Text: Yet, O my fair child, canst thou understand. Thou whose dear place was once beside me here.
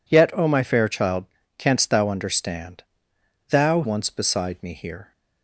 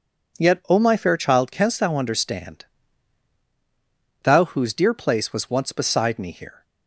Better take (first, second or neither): second